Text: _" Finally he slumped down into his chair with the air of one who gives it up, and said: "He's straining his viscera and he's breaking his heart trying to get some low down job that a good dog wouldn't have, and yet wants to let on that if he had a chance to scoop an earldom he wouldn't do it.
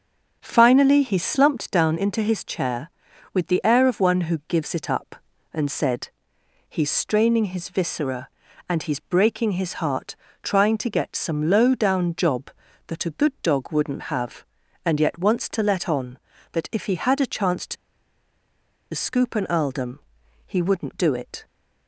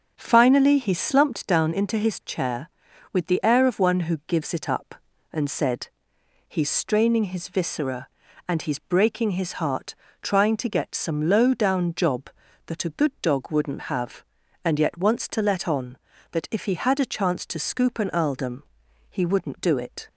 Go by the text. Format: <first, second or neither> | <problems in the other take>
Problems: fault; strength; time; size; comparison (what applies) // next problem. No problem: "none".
second | starts louder than the rest; until 1.4 s; 6.5 dB; also in the second // pauses between "heart" and "trying"; slight; at 10.1 s; 0.26 s long; slight in the second // pauses between "to" and "scoop"; at 17.7 s; 1.1 s long // pauses between "earldom" and "he"; noticeable; at 19.9 s; 0.48 s long; noticeable in the second